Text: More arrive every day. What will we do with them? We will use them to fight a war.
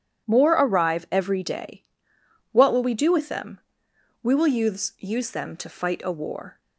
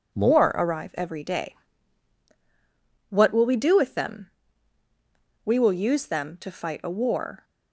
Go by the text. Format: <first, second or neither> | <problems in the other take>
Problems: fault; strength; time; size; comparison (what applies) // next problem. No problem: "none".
second | says "use" twice; at 4.9 s